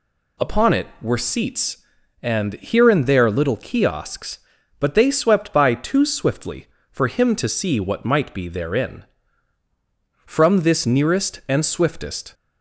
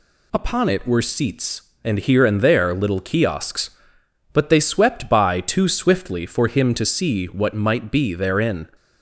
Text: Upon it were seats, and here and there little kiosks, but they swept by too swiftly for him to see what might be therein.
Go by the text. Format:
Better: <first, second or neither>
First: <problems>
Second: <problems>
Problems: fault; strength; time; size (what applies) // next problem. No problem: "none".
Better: second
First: goes on to say "From this nearest and swiftest"; strong; from 10.2 s on; 2.0 s long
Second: none